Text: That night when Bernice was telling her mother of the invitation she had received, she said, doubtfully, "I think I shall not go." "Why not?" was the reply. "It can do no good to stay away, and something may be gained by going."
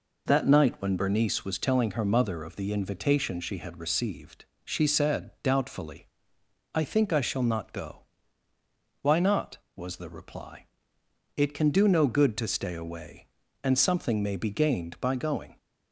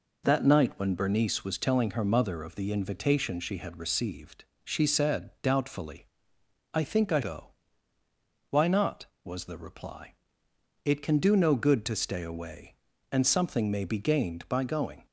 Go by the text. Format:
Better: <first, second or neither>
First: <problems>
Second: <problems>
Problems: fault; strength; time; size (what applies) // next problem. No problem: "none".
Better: first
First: none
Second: skips "shall not"; at 7.2 s